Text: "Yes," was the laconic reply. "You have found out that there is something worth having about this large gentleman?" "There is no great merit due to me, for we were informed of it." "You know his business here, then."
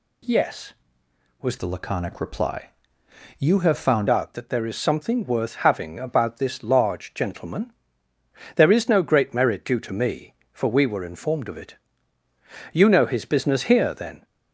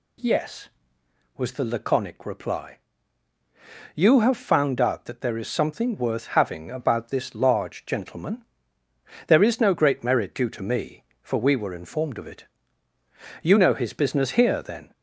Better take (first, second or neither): second